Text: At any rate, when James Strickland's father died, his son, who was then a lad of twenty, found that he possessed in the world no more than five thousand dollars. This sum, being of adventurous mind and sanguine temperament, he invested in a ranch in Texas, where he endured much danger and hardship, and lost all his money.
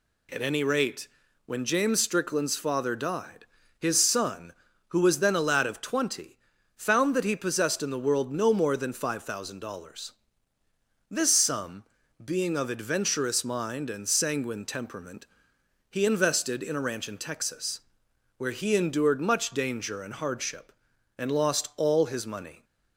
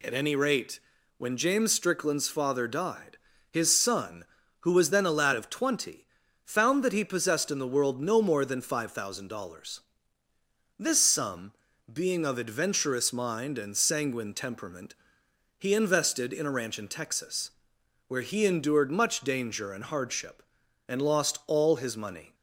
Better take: neither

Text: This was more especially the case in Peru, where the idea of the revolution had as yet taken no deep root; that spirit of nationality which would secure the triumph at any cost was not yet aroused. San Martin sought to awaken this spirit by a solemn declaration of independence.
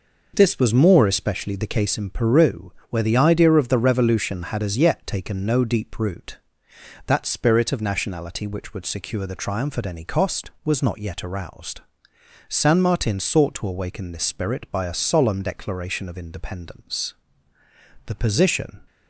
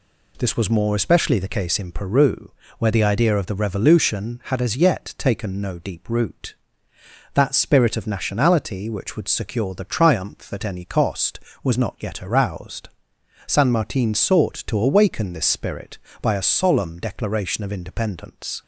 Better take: second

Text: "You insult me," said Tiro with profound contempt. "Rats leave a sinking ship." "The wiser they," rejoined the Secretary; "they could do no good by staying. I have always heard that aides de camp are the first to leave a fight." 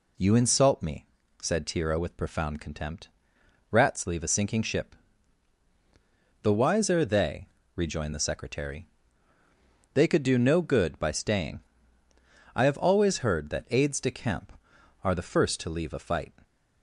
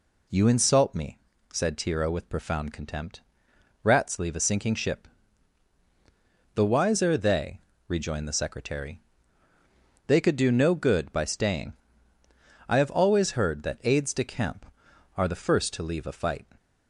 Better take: neither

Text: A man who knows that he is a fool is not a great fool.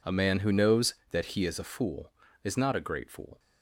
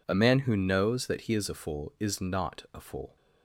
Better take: first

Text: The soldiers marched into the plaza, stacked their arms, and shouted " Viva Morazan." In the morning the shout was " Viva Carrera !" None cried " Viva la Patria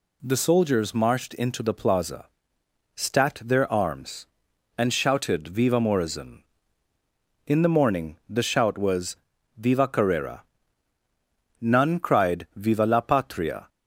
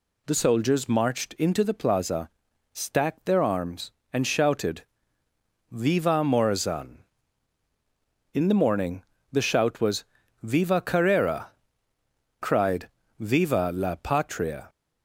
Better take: first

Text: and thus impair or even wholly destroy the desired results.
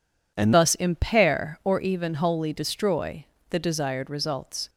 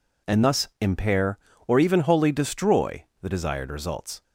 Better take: second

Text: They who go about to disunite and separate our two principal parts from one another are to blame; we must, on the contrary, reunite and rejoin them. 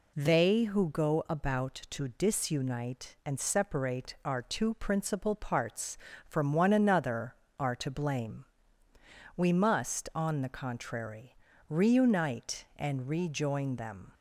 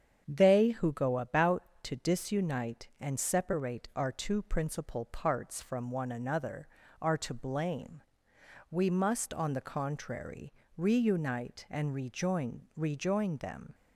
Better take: first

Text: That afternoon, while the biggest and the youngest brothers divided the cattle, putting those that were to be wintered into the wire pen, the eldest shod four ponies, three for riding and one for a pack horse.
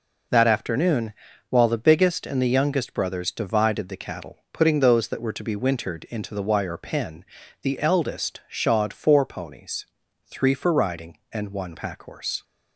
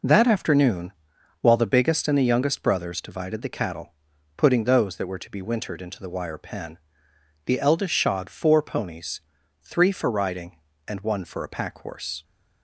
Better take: second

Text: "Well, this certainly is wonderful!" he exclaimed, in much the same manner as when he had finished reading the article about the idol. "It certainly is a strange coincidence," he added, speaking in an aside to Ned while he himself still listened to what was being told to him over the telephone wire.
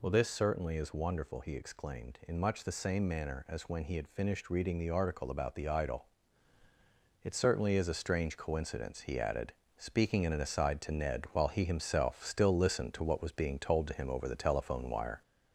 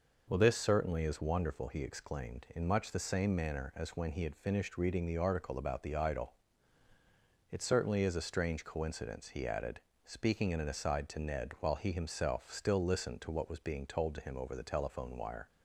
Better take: second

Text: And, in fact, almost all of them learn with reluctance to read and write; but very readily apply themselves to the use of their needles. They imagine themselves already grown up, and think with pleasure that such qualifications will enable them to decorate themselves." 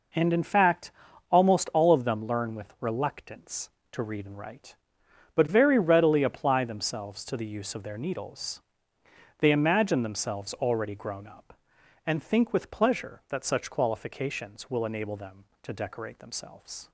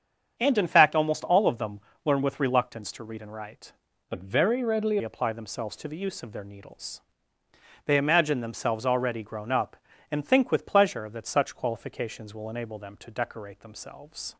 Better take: first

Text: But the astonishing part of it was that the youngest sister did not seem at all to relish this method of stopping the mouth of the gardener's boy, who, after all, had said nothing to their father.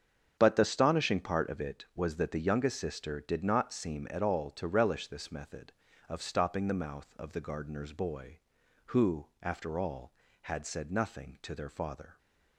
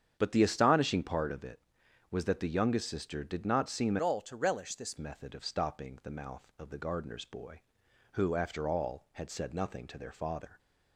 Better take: first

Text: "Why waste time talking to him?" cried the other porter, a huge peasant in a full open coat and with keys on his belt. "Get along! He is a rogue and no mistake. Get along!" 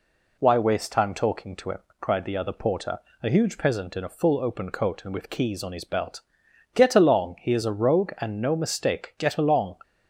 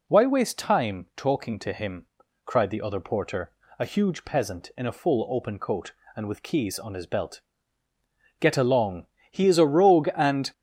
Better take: first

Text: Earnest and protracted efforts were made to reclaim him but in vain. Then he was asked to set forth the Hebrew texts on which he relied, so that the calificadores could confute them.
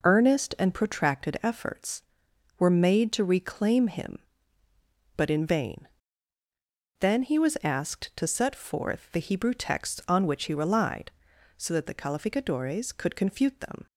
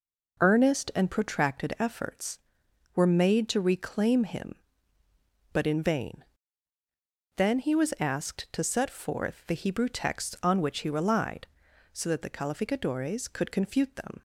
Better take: neither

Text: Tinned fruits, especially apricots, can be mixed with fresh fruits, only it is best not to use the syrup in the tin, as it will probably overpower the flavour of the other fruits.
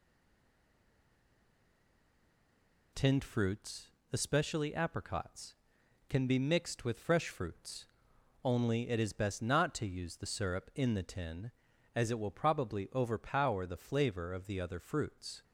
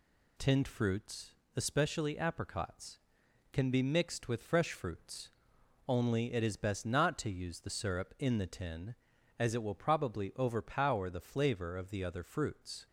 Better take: second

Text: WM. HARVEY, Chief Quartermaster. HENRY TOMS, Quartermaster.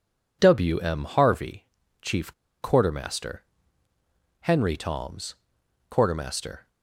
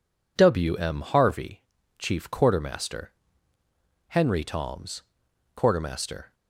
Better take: second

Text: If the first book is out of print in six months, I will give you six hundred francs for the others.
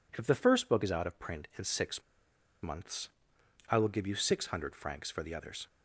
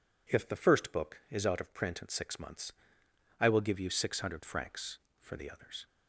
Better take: second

